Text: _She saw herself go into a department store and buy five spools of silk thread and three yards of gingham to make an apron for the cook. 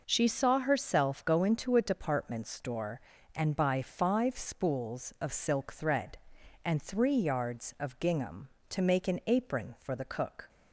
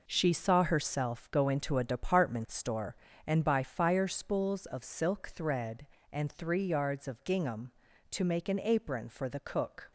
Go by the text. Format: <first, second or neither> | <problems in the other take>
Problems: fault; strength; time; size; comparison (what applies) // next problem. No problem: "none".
first | says "fire" for "five"; at 3.6 s